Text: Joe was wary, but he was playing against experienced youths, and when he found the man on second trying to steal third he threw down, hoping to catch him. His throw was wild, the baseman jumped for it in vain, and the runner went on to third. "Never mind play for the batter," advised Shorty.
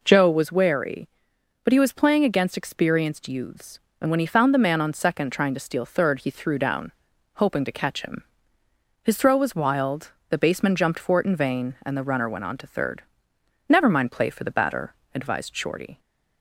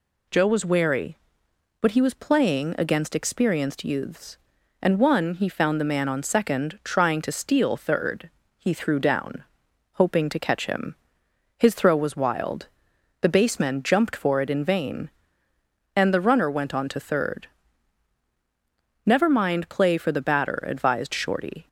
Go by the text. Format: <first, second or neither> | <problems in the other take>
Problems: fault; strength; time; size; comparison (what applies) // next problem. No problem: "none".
first | says "one" for "when"; at 4.9 s // pauses between "third" and "he"; slight; at 8.2 s; 0.30 s long